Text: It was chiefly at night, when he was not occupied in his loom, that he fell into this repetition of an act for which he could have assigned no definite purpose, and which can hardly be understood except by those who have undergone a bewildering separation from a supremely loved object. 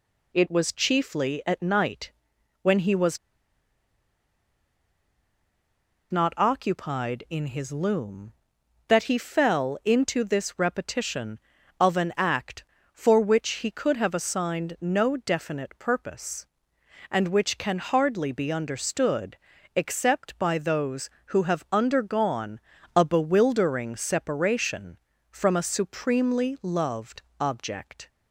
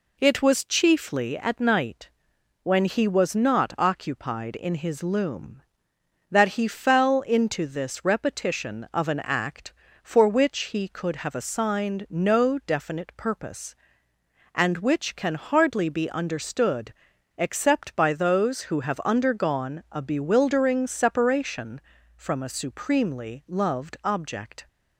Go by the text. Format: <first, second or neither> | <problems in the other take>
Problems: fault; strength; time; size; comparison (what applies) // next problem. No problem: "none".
second | pauses between "was" and "not"; strong; at 3.1 s; 2.9 s long // pauses between "understood" and "except"; at 19.3 s; 0.40 s long; also in the second // pauses between "undergone" and "a"; at 22.5 s; 0.38 s long // pauses between "loved" and "object"; slight; at 27.2 s; 0.16 s long